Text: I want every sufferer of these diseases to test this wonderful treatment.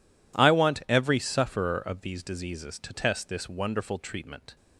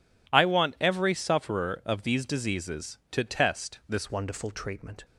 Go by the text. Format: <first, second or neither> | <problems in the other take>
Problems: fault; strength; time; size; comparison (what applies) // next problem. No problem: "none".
first | changes voice at "wonderful"; from 4.1 s on; 0.9 s long